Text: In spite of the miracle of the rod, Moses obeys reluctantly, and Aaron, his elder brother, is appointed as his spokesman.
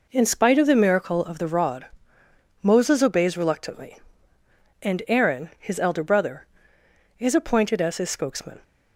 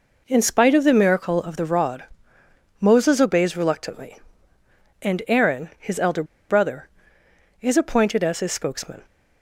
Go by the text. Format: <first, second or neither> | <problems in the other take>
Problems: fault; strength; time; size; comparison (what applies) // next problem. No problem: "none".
first | pauses between "elder" and "brother"; slight; at 6.2 s; 0.25 s long